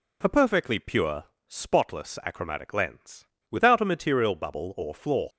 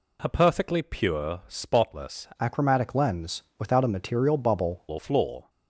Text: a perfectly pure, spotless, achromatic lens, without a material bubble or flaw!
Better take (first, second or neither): first